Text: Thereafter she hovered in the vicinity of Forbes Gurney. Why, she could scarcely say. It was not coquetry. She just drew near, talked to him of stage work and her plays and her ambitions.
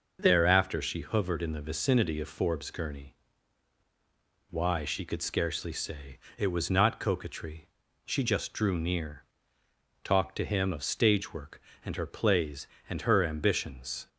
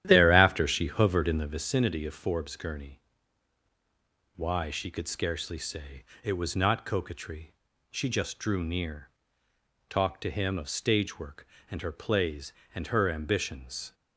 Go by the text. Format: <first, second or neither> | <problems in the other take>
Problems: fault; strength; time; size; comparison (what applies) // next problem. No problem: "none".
first | starts louder than the rest; strong; until 1.6 s; 11.5 dB